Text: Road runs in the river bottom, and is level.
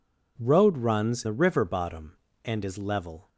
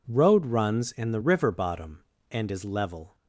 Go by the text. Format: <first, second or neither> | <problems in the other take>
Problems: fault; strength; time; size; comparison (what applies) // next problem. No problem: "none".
second | skips "in"; at 1.2 s